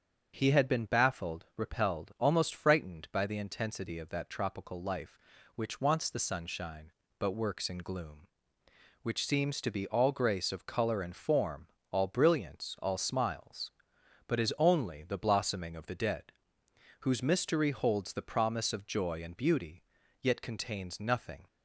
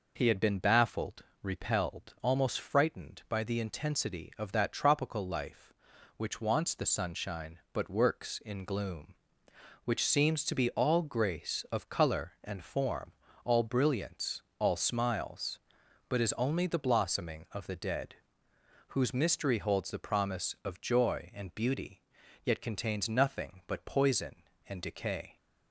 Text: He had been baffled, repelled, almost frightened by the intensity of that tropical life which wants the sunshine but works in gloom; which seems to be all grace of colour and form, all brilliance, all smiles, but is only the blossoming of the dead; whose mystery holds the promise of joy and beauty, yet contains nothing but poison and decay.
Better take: second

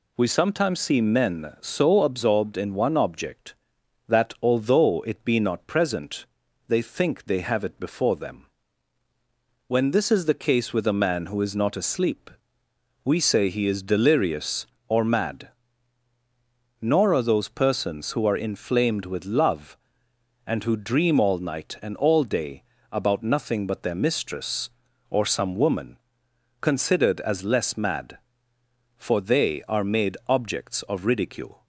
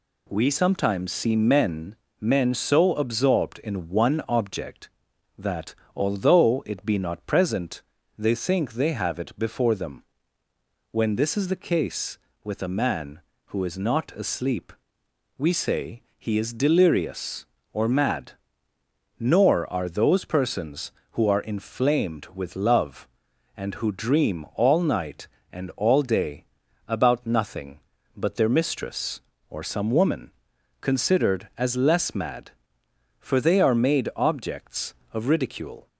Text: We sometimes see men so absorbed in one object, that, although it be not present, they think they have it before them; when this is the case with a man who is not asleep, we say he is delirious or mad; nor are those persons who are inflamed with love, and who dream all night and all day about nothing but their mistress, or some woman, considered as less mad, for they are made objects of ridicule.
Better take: first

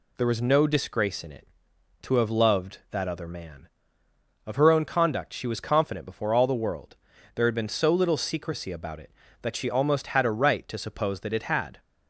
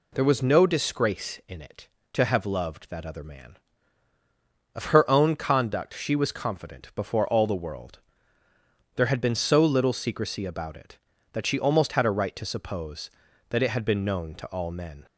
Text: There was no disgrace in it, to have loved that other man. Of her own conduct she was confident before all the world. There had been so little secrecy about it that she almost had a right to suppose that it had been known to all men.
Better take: second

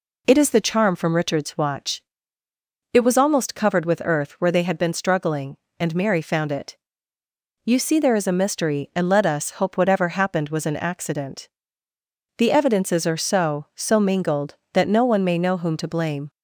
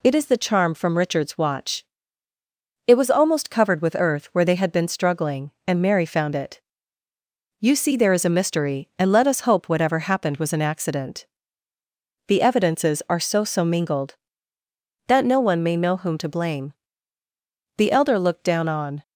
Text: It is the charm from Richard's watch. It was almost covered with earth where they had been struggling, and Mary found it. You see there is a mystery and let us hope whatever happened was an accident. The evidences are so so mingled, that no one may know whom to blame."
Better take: first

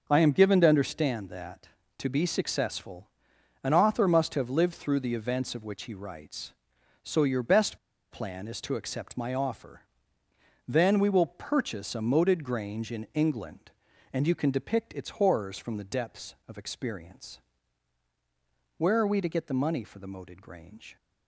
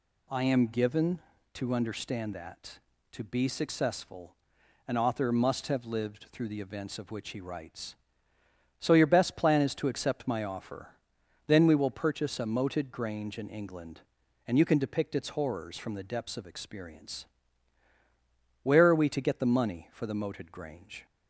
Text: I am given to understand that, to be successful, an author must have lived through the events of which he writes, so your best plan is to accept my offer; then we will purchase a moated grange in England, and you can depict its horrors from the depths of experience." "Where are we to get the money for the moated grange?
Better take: second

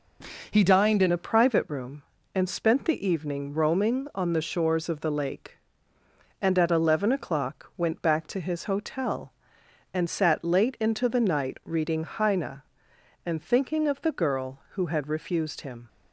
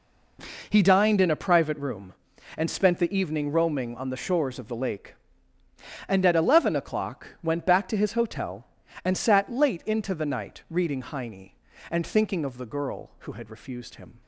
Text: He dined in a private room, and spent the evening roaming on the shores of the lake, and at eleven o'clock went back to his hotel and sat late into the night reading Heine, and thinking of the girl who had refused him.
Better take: second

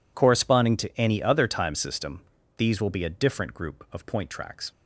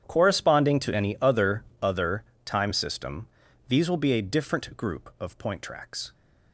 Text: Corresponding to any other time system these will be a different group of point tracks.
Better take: first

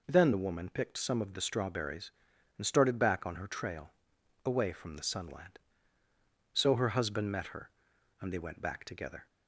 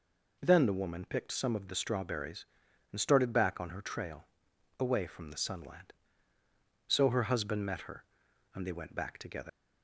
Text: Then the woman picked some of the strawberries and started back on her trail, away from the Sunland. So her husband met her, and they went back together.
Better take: first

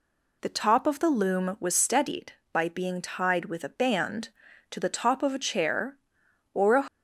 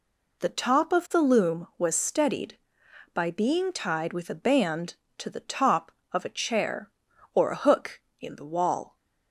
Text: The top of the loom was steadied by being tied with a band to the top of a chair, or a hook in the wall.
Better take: second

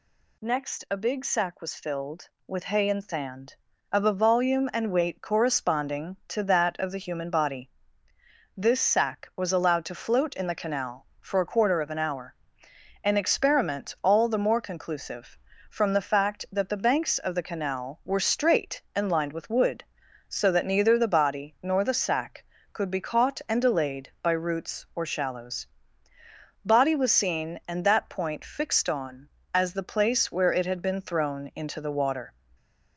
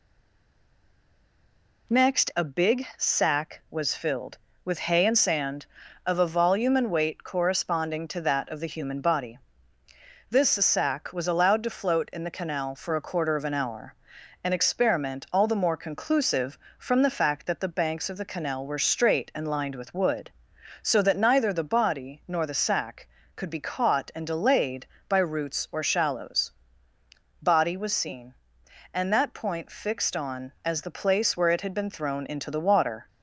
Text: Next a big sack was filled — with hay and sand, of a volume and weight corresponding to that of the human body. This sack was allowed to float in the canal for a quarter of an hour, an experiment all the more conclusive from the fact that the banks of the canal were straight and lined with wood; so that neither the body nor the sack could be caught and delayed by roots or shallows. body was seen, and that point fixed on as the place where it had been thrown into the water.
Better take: first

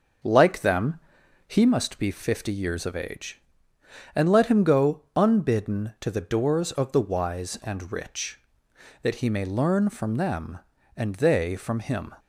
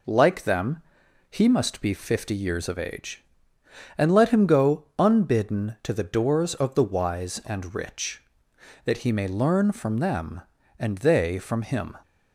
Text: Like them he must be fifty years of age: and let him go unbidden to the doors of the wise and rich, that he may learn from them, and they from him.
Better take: second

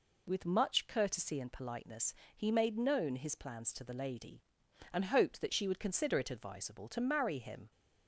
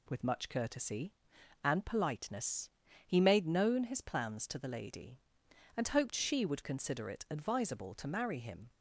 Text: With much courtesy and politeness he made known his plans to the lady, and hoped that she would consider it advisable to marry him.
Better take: first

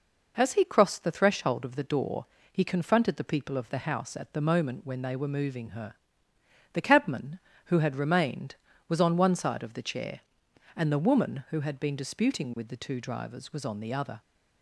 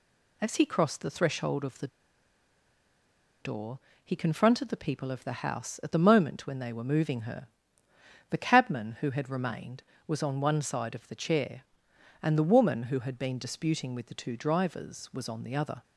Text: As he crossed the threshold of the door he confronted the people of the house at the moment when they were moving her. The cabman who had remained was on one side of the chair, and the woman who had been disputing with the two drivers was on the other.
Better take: first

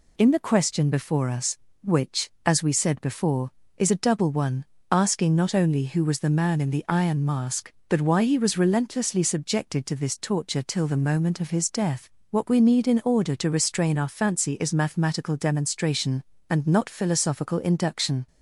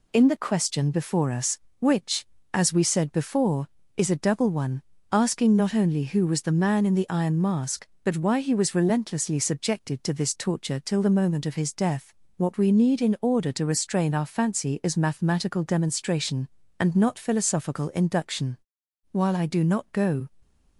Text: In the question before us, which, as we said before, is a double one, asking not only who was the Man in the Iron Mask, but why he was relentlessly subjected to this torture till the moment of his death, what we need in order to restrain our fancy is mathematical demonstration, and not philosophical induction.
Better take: first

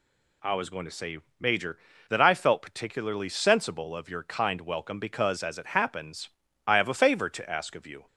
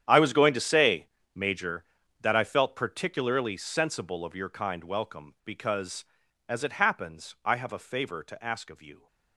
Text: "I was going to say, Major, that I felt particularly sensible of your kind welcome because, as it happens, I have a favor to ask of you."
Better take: first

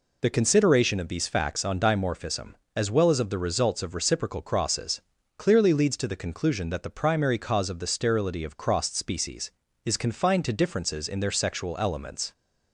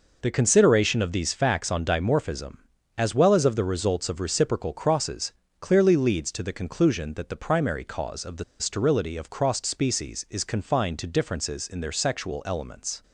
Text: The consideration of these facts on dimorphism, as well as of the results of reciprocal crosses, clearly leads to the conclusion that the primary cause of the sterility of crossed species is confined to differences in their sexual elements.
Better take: first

